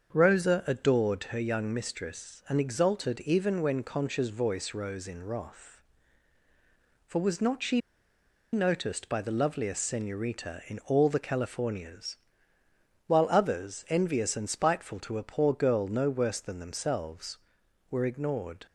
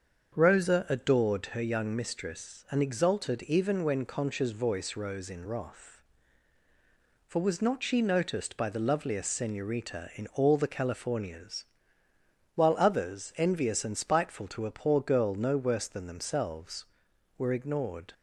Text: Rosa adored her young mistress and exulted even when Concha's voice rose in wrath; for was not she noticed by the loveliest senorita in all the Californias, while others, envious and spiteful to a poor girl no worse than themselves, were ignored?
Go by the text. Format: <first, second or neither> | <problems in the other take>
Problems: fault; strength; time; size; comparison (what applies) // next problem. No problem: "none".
second | starts louder than the rest; until 1.2 s; 7 dB; also in the second // pauses between "she" and "noticed"; noticeable; at 7.7 s; 0.73 s long